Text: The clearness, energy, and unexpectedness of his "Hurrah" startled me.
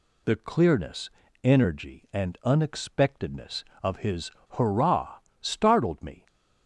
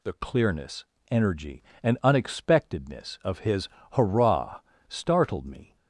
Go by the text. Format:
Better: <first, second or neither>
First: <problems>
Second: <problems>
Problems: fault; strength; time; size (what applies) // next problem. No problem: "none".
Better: neither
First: pauses between "his" and "Hurrah"; slight; at 4.3 s; 0.19 s long // pauses between "Hurrah" and "startled"; slight; at 5.1 s; 0.22 s long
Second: pauses between "his" and "Hurrah"; slight; at 3.6 s; 0.24 s long // pauses between "Hurrah" and "startled"; slight; at 4.5 s; 0.28 s long